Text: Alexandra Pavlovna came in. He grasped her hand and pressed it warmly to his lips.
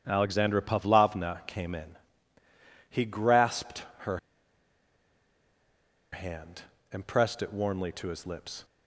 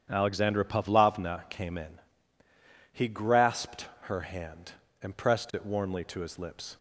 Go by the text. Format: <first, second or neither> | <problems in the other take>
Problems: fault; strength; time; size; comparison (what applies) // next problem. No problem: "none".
second | starts louder than the rest; strong; until 1.0 s; 9 dB; strong in the second // pauses between "grasped" and "her"; slight; at 3.8 s; 0.16 s long; slight in the second // pauses between "her" and "hand"; strong; at 4.1 s; 1.9 s long